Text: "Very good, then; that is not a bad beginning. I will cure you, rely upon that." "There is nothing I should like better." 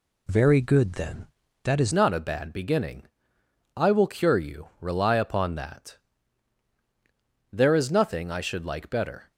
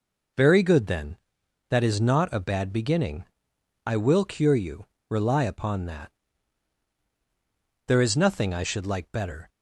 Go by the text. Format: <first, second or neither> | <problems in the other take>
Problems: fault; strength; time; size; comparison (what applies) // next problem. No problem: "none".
second | changes voice at "not"; from 1.9 s on; 7.4 s long